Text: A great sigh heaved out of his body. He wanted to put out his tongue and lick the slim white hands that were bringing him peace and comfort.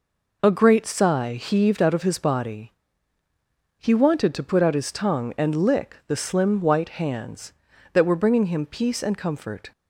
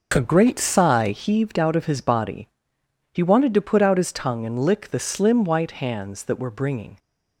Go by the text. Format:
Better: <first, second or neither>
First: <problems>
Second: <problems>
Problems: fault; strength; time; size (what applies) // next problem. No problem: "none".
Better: first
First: none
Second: stops before "him peace and comfort"; at 6.9 s